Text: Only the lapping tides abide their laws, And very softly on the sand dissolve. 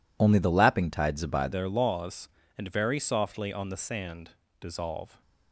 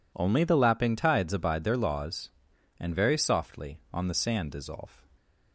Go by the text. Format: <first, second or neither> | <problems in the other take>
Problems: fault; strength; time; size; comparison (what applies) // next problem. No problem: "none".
second | changes voice at "their"; from 1.5 s on; 3.7 s long // pauses between "sand" and "dissolve"; slight; at 4.3 s; 0.30 s long